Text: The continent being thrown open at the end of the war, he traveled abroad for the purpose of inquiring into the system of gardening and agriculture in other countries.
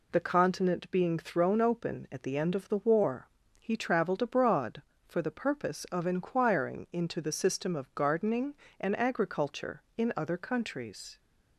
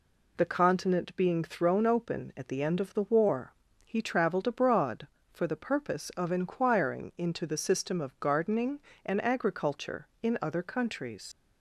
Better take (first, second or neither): first